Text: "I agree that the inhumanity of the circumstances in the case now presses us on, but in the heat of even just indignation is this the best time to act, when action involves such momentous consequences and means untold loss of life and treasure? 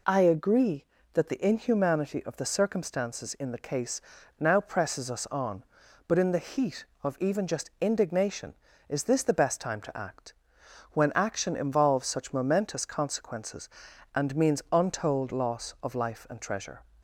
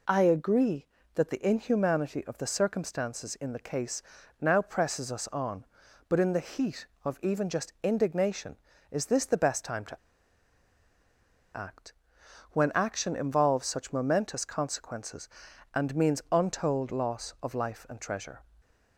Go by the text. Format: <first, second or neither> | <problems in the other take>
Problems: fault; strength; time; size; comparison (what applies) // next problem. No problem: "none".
first | pauses between "case" and "now"; at 4.0 s; 0.38 s long; also in the first // pauses between "to" and "act"; strong; at 9.9 s; 1.5 s long